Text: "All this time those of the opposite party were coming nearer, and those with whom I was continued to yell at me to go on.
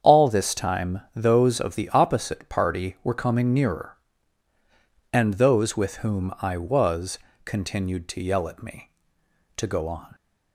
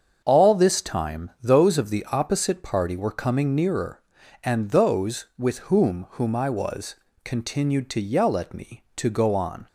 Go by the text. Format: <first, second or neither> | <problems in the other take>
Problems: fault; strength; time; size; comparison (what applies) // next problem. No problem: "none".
first | starts louder than the rest; until 1.2 s; 7 dB; strong in the first // says "whom" twice; at 6.1 s // pauses between "was" and "continued"; slight; at 6.9 s; 0.30 s long; slight in the first